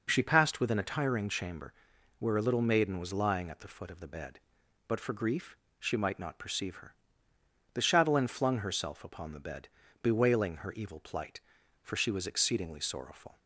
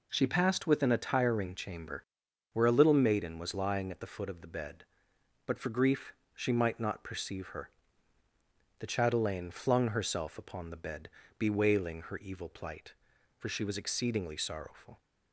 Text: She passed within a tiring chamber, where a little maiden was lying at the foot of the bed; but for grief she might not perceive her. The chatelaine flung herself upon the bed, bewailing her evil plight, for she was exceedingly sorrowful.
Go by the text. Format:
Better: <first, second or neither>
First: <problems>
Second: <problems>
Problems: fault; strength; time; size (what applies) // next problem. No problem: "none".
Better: neither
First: pauses between "grief" and "she"; slight; at 5.5 s; 0.24 s long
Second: pauses between "grief" and "she"; slight; at 6.1 s; 0.20 s long